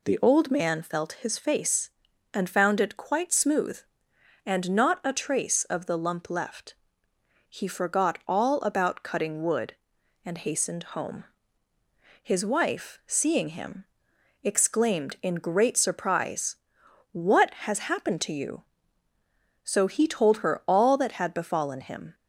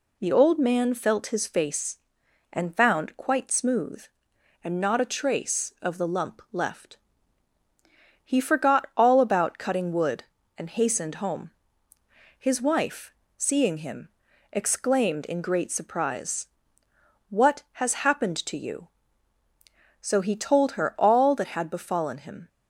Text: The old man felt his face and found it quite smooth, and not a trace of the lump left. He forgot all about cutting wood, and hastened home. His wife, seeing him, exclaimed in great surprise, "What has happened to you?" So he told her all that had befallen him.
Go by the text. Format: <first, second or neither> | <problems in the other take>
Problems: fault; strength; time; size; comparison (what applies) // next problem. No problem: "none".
first | skips "it"; at 3.1 s